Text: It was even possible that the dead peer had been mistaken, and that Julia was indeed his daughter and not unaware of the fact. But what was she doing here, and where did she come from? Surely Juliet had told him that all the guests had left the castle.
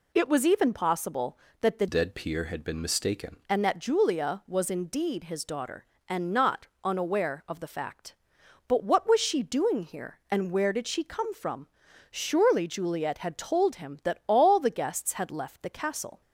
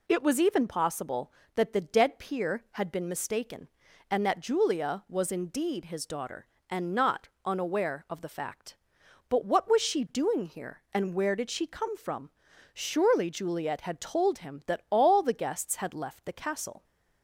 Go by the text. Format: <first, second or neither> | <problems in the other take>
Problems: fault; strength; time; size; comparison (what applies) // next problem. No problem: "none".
second | changes voice from "dead" to "mistaken"; from 1.8 to 3.3 s; 1.5 s long // pauses between "not" and "unaware"; slight; at 6.6 s; 0.16 s long; slight in the second